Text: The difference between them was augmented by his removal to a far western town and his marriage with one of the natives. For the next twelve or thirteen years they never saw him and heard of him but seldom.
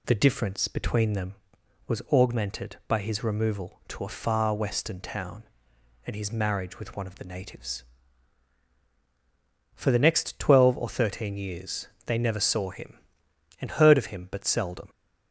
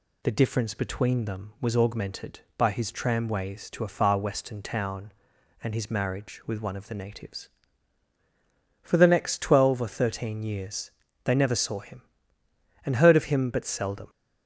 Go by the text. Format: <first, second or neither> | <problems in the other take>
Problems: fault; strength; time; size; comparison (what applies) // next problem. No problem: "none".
first | says "tramways" for "removal"; at 2.9 s // pauses between "years" and "they"; slight; at 10.9 s; 0.32 s long; slight in the first